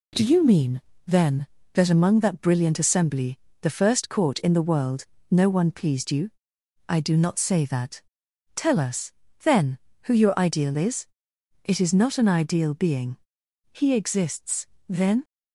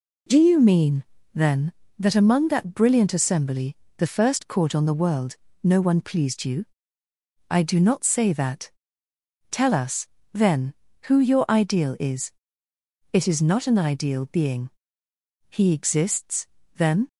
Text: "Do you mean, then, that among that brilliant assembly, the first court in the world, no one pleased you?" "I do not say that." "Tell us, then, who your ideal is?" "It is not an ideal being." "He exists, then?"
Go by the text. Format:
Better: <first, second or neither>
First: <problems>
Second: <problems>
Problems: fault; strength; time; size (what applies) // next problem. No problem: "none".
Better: first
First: none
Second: says "on" for "in"; at 4.7 s